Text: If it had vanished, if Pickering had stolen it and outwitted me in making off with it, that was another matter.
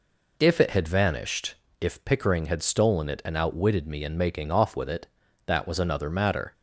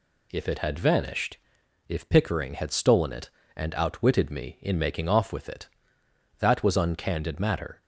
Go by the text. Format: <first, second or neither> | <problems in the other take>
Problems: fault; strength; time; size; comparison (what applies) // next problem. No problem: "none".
first | says "uncandid" for "another"; at 6.7 s